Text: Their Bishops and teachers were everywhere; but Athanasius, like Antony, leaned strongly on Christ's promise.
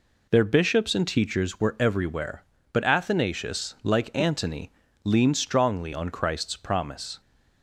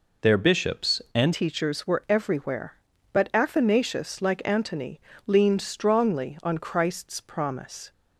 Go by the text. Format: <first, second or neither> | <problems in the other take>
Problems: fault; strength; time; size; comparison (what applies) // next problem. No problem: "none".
first | changes voice at "teachers"; from 1.3 s on; 6.6 s long